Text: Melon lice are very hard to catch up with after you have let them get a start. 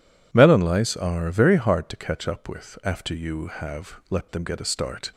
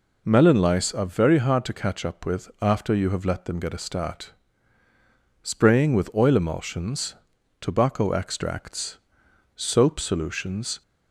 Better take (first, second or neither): first